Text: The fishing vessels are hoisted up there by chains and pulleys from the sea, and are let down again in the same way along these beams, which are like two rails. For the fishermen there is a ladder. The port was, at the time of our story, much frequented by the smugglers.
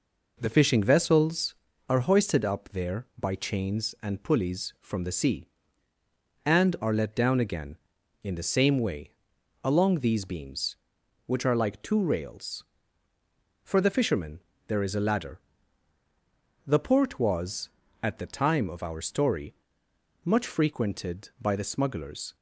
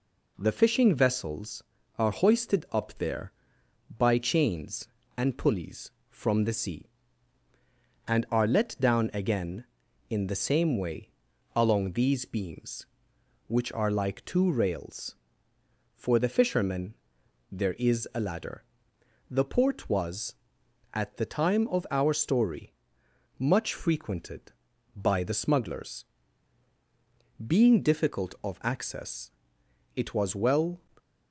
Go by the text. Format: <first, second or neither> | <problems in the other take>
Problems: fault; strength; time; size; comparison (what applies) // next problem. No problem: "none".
first | pauses between "way" and "along"; at 11.1 s; 0.44 s long; noticeable in the first // pauses between "fishermen" and "there"; noticeable; at 16.9 s; 0.56 s long; slight in the first // goes on to say "Being difficult of access it was well"; strong; from 27.4 s on; 3.3 s long